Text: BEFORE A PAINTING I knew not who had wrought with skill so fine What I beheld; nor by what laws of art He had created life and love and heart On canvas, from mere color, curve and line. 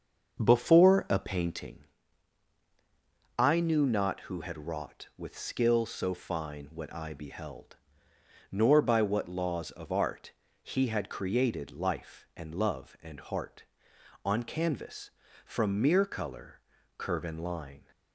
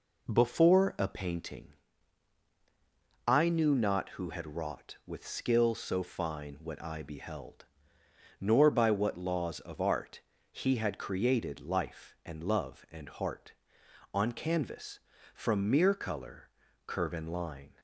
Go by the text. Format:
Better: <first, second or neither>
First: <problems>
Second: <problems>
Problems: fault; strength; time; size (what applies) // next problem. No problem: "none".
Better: second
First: starts louder than the rest; until 1.8 s; 7 dB // pauses between "PAINTING" and "I"; strong; at 1.8 s; 1.5 s long // pauses between "art" and "He"; slight; at 10.3 s; 0.32 s long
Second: pauses between "PAINTING" and "I"; strong; at 1.7 s; 1.5 s long // pauses between "art" and "He"; slight; at 10.1 s; 0.32 s long